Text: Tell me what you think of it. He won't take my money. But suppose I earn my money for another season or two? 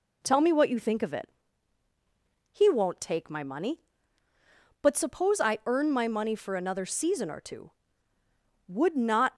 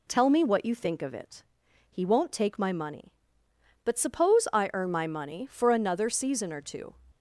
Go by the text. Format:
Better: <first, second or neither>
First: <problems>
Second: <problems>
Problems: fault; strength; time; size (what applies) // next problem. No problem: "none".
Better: second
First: goes on to say "Would not"; noticeable; from 8.6 s on; 0.68 s long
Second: none